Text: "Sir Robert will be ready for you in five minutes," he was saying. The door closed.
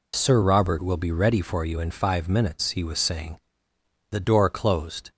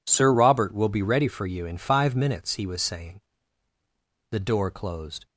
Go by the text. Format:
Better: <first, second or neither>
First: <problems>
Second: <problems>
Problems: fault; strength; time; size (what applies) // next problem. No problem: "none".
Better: second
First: loses the start of "Sir"; at 0.1 s; 40 ms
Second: none